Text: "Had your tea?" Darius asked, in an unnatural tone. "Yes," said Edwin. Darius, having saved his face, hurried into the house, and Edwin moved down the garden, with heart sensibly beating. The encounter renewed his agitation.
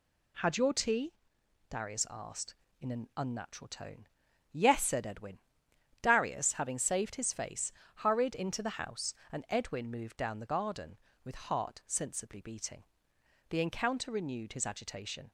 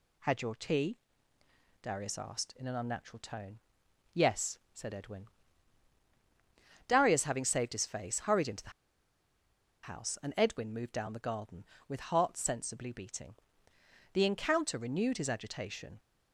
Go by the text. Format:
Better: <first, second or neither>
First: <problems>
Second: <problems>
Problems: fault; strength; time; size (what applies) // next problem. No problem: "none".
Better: first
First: none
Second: pauses between "the" and "house"; at 8.7 s; 1.1 s long